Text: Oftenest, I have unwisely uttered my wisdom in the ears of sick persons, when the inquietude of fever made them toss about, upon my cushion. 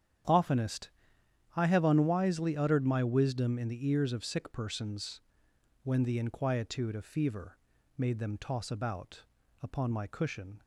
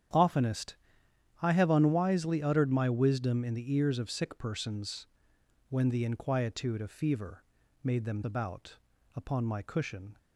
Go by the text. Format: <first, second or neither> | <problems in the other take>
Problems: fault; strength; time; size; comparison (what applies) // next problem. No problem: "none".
first | starts louder than the rest; strong; until 1.7 s; 9.5 dB; strong in the first // pauses between "fever" and "made"; at 7.4 s; 0.38 s long; also in the first // skips "toss"; at 8.2 s